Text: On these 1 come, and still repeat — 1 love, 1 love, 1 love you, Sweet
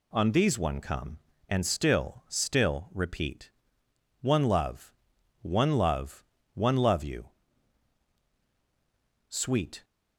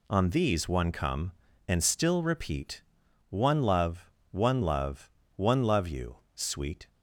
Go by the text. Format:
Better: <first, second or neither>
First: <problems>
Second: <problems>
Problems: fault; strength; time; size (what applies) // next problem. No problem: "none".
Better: second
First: says "still" twice; at 2.2 s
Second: none